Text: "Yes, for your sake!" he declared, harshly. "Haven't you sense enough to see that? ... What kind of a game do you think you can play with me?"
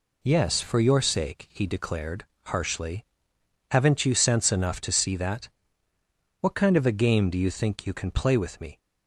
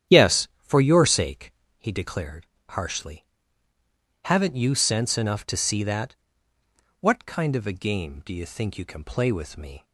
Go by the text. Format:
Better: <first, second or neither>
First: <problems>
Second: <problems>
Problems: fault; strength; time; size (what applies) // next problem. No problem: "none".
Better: first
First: none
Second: starts louder than the rest; strong; until 1.9 s; 10 dB